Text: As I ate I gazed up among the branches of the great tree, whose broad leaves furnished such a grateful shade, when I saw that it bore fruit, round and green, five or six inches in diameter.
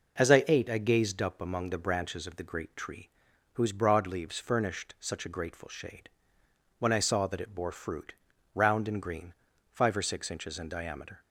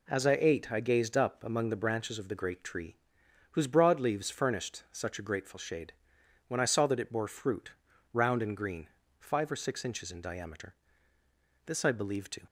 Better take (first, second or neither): first